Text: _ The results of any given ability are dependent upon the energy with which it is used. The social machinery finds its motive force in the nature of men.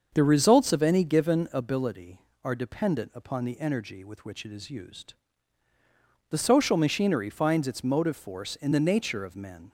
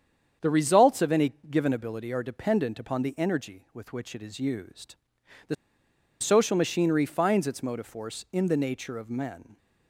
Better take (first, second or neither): first